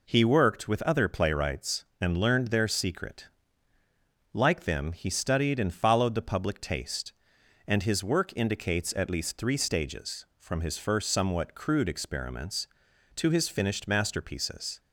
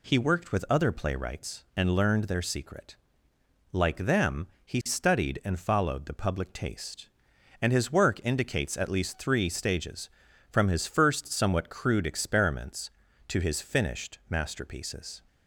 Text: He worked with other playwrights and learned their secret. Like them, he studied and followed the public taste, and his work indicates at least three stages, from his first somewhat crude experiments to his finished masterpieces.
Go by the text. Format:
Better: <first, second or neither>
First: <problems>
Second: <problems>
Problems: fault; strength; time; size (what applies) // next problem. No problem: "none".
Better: neither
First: none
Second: none